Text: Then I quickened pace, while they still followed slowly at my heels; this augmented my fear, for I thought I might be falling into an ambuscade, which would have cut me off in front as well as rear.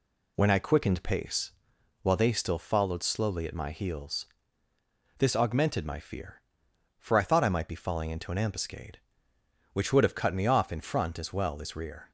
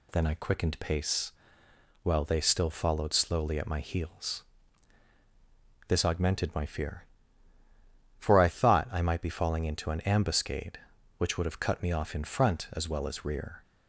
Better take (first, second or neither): second